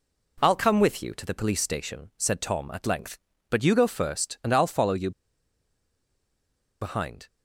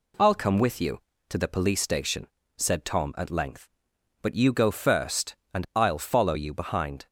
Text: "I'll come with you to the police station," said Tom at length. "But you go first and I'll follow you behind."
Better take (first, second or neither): second